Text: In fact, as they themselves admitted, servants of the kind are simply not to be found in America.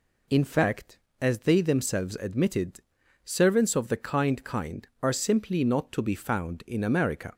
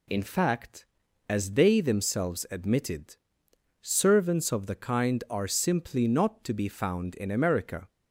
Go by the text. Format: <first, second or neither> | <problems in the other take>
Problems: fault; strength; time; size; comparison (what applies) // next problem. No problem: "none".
second | says "kind" twice; at 4.4 s